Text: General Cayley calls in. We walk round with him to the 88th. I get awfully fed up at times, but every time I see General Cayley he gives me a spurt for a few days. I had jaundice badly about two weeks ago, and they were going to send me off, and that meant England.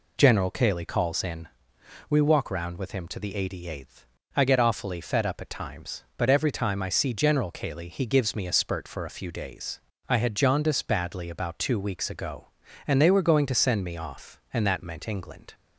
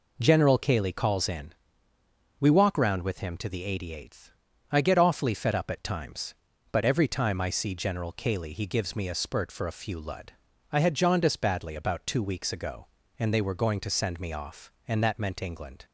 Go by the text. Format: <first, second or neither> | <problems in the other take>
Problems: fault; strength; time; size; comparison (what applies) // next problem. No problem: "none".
first | says "lud" for "days"; at 9.9 s